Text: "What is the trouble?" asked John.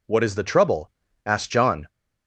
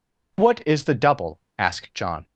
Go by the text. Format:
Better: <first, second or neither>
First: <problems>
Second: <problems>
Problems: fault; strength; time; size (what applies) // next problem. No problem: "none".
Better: first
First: none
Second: says "double" for "trouble"; at 0.9 s